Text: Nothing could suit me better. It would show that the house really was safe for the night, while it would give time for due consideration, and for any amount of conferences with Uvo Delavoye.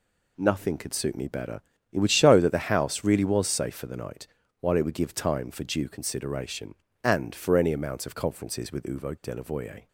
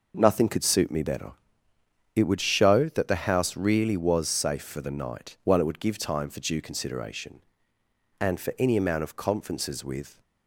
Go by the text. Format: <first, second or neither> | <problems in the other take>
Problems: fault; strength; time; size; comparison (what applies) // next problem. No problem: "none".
first | stops before "Uvo Delavoye"; at 10.2 s